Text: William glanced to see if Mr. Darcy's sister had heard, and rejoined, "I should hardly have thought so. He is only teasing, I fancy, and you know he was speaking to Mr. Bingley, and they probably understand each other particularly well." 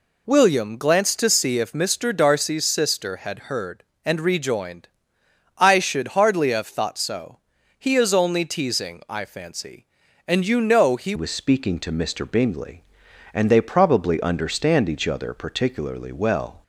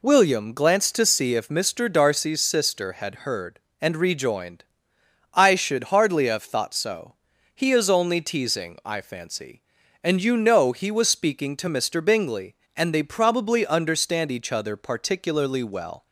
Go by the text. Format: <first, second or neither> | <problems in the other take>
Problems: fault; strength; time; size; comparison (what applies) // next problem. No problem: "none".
second | changes voice at "was"; from 11.1 s on; 5.5 s long